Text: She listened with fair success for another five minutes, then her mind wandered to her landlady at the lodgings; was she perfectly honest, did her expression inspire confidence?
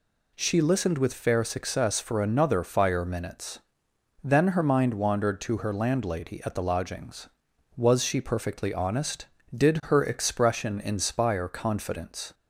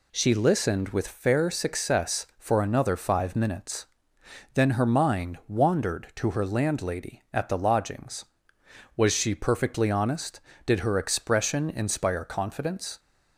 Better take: second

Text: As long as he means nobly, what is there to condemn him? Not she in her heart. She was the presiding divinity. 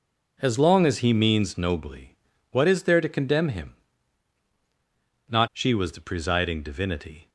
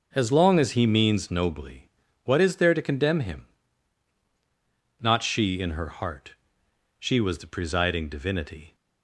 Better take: second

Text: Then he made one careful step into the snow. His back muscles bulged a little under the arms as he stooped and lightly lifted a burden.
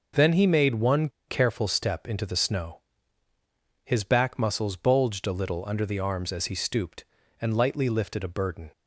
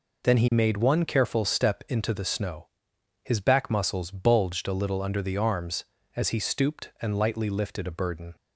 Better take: second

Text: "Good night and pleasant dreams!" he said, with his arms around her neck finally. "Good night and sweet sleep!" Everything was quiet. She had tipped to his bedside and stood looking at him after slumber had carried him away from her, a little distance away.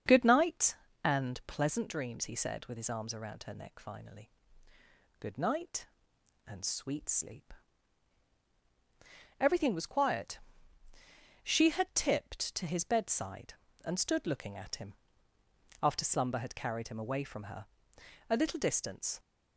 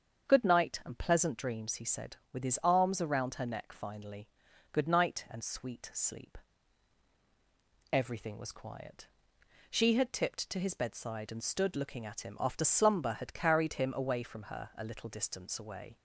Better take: second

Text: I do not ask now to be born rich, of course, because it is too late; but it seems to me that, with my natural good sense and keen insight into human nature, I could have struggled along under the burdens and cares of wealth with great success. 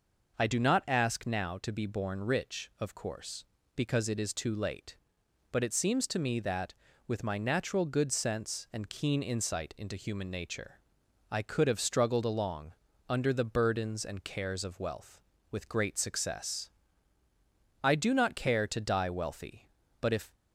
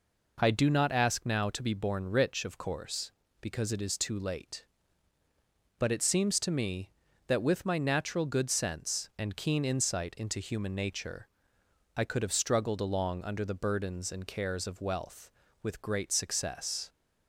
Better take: second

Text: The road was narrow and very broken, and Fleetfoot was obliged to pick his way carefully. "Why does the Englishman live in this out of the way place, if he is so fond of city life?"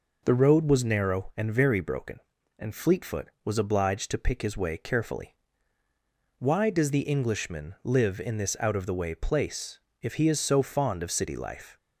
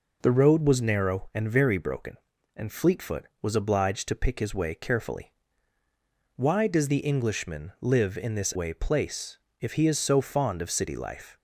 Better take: first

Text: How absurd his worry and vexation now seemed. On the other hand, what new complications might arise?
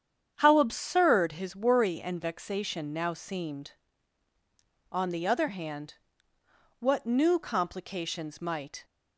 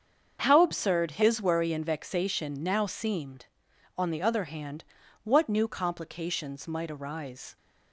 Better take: second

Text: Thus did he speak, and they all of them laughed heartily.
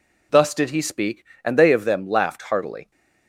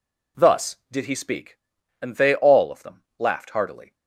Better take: second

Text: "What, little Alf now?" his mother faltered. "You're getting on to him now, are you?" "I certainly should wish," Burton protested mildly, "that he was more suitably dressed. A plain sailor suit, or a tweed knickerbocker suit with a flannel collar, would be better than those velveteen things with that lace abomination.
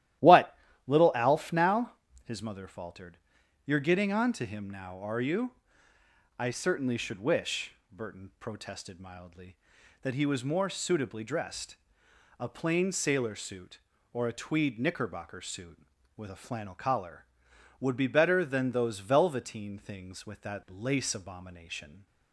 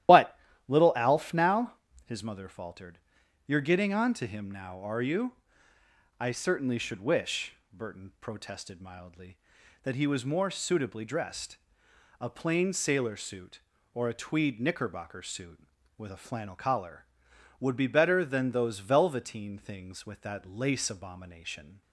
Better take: first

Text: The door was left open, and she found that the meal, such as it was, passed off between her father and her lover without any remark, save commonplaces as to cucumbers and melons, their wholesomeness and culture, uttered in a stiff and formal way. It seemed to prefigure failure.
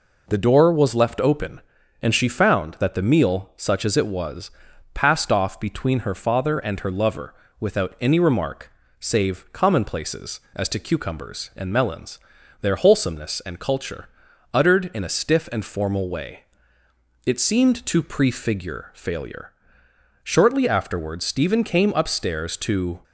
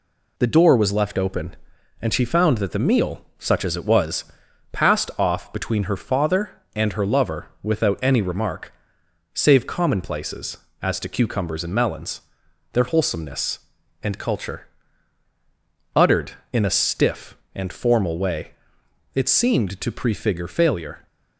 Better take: second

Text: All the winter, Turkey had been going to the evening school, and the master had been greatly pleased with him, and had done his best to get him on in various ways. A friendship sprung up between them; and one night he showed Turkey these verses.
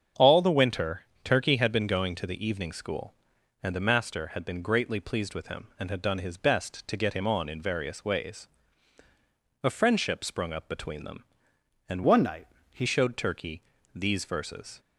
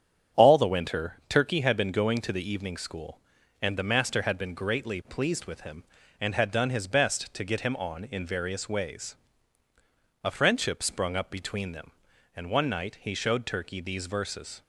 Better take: second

